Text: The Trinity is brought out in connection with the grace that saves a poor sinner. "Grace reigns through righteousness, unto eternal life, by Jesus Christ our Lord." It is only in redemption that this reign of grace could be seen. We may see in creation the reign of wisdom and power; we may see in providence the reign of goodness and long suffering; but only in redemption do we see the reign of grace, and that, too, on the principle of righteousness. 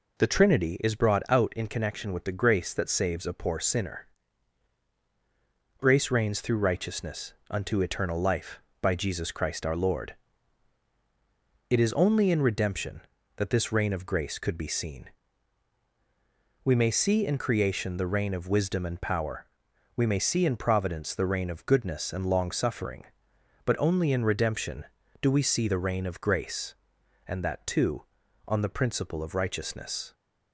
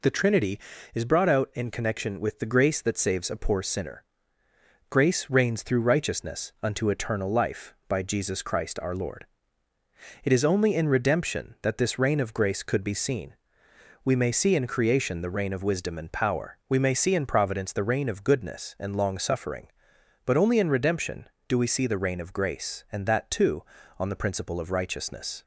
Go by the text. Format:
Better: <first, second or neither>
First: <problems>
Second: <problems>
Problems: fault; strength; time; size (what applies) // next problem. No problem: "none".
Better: neither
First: none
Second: none